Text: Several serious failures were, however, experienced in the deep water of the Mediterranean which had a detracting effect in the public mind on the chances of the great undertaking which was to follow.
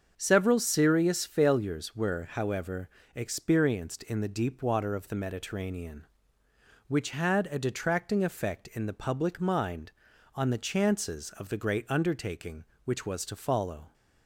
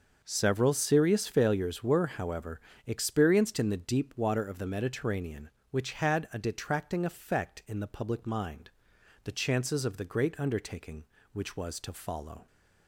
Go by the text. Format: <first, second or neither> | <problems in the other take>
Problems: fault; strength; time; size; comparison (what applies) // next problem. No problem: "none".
first | starts louder than the rest; until 1.2 s; 6.5 dB; also in the first // skips "on"; at 8.9 s